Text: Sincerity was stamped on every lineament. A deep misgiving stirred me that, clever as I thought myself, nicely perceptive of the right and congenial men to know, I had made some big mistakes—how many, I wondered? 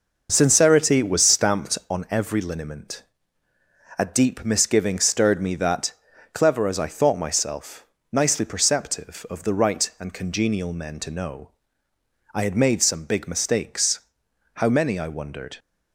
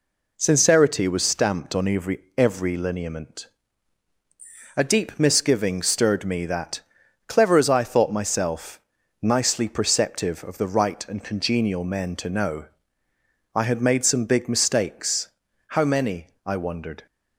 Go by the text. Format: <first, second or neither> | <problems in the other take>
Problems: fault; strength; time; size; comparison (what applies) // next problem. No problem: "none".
first | says "every" twice; at 2.3 s